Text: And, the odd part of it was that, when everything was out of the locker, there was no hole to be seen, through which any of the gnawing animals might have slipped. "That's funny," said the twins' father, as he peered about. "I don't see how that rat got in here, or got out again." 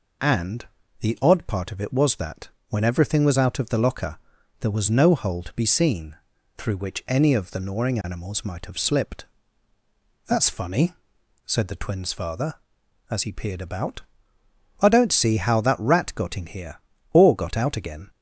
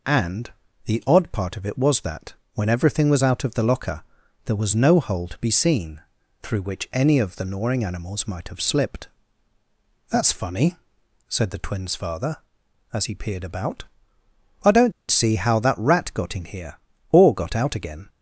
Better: first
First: none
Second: pauses between "don't" and "see"; slight; at 14.9 s; 0.18 s long

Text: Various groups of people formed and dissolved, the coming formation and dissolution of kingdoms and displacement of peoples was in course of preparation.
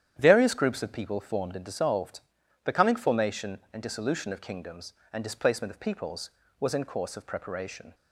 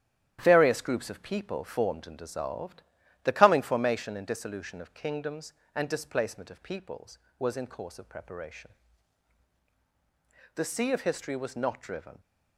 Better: first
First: starts louder than the rest; strong; until 1.1 s; 10 dB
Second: starts louder than the rest; strong; until 1.4 s; 10.5 dB // goes on to say "The sea of history was not driven"; from 10.5 s on; 1.6 s long

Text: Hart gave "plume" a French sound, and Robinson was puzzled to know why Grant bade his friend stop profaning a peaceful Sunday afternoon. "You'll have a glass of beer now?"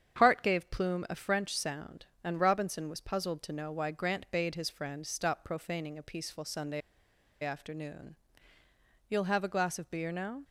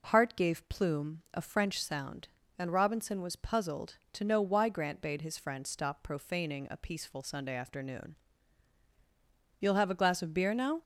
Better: second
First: starts louder than the rest; strong; until 1.2 s; 8 dB // pauses between "Sunday" and "afternoon"; noticeable; at 6.8 s; 0.62 s long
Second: none

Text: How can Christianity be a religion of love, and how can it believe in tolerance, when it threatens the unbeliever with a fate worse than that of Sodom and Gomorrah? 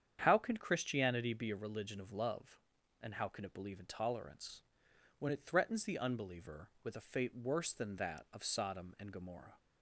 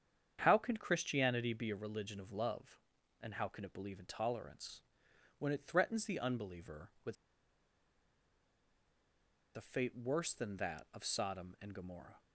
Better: first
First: starts louder than the rest; strong; until 1.2 s; 8.5 dB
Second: starts louder than the rest; strong; until 1.4 s; 8.5 dB // pauses between "with" and "a"; strong; at 7.1 s; 2.4 s long

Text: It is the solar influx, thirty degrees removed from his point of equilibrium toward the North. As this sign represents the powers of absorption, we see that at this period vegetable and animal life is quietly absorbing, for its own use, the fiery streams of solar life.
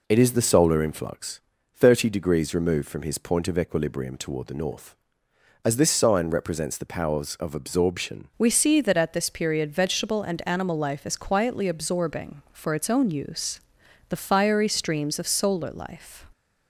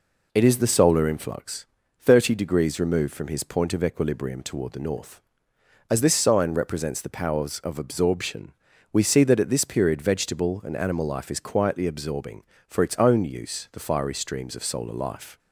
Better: second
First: changes voice at "we"; from 8.4 s on; 7.8 s long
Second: none

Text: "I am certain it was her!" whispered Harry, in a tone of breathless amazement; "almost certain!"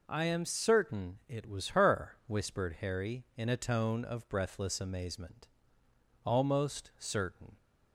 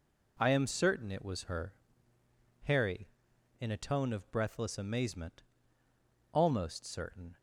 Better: first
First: none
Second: skips "whispered"; at 2.1 s

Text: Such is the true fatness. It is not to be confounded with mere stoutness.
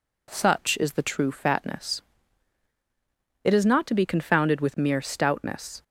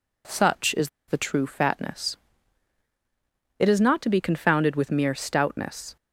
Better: first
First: none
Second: pauses between "is" and "the"; slight; at 0.8 s; 0.18 s long

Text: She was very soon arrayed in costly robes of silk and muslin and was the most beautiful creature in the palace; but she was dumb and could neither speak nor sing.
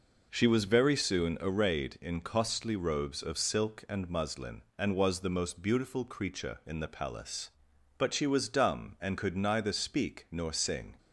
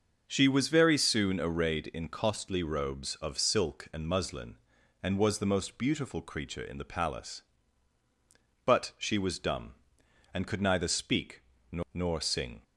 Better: first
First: none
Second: starts louder than the rest; noticeable; until 1.2 s; 6 dB // pauses between "speak" and "nor"; slight; at 11.4 s; 0.28 s long // says "nor" twice; at 11.9 s

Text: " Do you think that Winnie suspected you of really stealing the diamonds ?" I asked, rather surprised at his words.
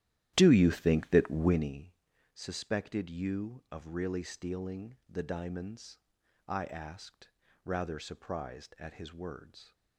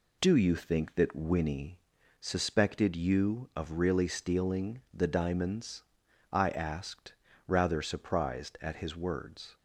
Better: second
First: starts louder than the rest; strong; until 1.8 s; 13 dB // pauses between "Winnie" and "suspected"; at 1.9 s; 0.38 s long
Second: pauses between "Winnie" and "suspected"; at 1.7 s; 0.40 s long

